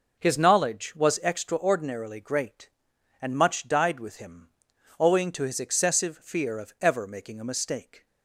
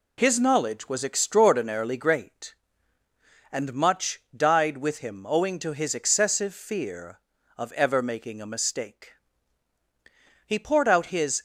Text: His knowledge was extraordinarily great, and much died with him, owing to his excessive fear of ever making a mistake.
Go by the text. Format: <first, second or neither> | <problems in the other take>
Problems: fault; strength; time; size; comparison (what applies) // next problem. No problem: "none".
first | goes on to say "He poured out his"; noticeable; from 10.4 s on; 0.98 s long